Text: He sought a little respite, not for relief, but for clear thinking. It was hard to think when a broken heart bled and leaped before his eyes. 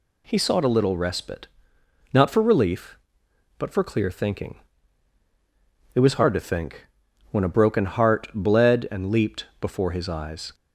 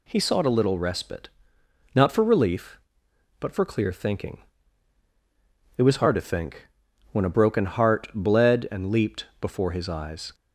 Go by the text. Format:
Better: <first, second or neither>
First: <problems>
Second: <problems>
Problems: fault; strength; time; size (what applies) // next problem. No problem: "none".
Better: neither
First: pauses between "think" and "when"; at 6.8 s; 0.44 s long // pauses between "leaped" and "before"; slight; at 9.4 s; 0.16 s long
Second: pauses between "think" and "when"; at 6.6 s; 0.44 s long // pauses between "leaped" and "before"; slight; at 9.2 s; 0.16 s long